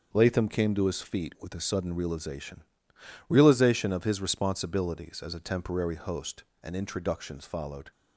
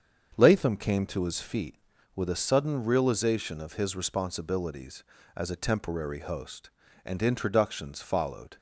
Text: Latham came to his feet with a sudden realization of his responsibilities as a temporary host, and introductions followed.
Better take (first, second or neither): second